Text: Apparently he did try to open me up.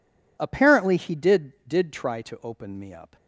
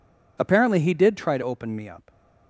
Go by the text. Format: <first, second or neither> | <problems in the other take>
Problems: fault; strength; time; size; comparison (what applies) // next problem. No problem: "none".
second | says "did" twice; at 1.6 s